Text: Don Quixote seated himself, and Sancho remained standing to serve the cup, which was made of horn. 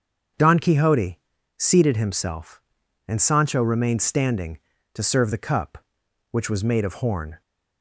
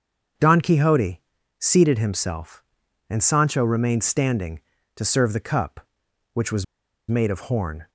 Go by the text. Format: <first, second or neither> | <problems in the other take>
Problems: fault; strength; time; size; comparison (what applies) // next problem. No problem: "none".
first | starts louder than the rest; until 1.7 s; 7 dB; also in the first // pauses between "Quixote" and "seated"; at 1.2 s; 0.38 s long; also in the first // pauses between "was" and "made"; at 6.6 s; 0.44 s long